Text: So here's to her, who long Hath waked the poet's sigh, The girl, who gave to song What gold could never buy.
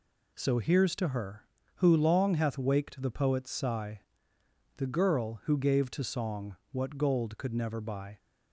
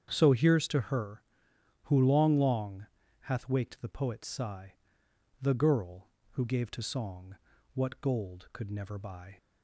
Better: first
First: pauses between "song" and "What"; slight; at 6.5 s; 0.16 s long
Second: starts louder than the rest; strong; until 1.1 s; 8 dB // says "long" twice; at 2.3 s // pauses between "song" and "What"; at 7.3 s; 0.40 s long

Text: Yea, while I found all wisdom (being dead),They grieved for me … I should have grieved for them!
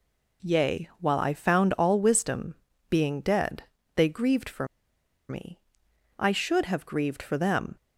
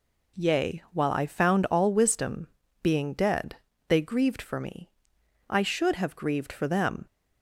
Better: second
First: pauses between "for" and "me"; noticeable; at 4.6 s; 0.63 s long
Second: none

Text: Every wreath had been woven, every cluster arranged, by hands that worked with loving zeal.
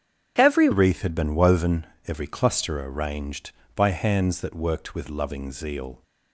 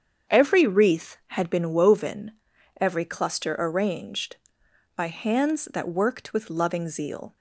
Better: second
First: starts louder than the rest; strong; until 1.3 s; 8 dB // changes voice at "wreath"; from 0.7 s on; 5.3 s long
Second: starts louder than the rest; strong; until 1.4 s; 7.5 dB

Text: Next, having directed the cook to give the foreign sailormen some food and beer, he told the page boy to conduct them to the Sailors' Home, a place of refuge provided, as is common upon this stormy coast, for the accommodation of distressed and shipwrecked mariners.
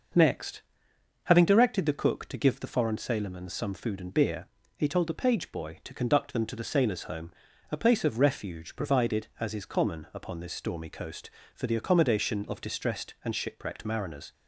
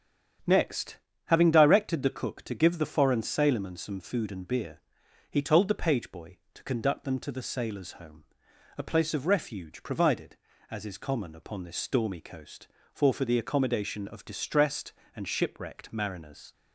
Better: first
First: starts louder than the rest; noticeable; until 1.7 s; 6 dB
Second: starts louder than the rest; strong; until 1.7 s; 9 dB // says "for" twice; at 13.1 s

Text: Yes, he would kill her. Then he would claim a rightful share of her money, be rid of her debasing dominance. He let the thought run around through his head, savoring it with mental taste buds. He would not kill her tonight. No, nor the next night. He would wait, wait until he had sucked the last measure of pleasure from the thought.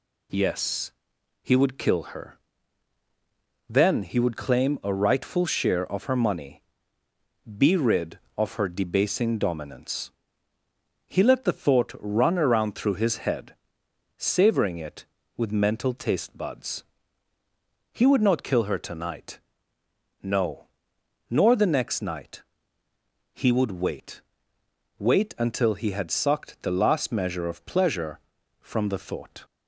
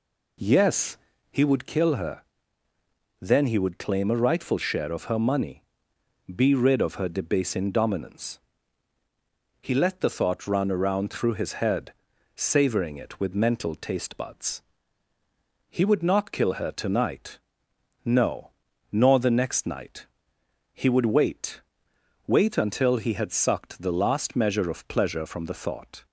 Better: first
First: none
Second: starts louder than the rest; slight; until 1.5 s; 2.5 dB

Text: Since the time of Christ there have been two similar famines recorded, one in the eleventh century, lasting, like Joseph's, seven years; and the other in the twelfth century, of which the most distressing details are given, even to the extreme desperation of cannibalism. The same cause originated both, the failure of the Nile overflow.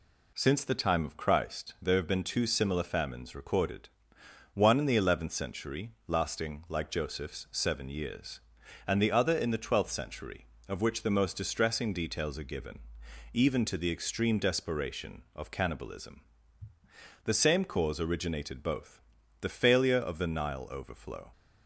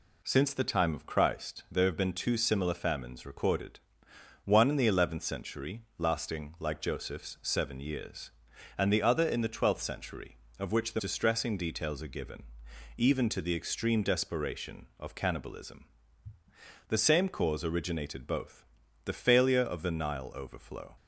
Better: first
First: none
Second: skips "most"; at 10.9 s

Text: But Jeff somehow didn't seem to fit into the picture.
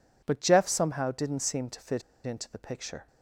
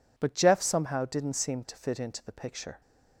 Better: second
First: pauses between "fit" and "into"; slight; at 2.0 s; 0.24 s long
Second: none

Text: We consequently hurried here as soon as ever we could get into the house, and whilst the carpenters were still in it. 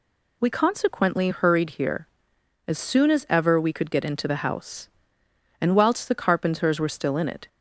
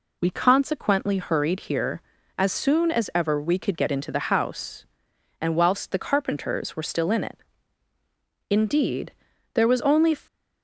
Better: first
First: none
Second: goes on to say "Indeed there was only"; from 8.4 s on; 1.6 s long

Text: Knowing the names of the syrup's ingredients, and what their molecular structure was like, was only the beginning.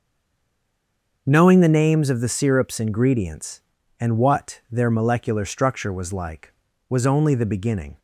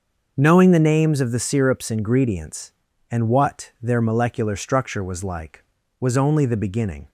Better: second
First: stays silent before the first word; noticeable; until 1.2 s; 1.2 s long // starts louder than the rest; until 2.2 s; 6 dB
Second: starts louder than the rest; until 1.3 s; 6 dB

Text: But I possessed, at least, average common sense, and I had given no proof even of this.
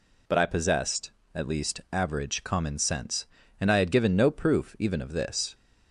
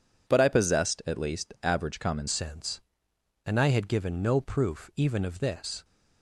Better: first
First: none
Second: changes voice at "sense"; from 2.2 s on; 3.6 s long

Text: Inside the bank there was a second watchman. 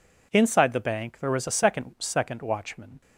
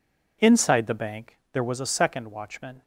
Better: second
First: says "second" twice; at 1.9 s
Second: none

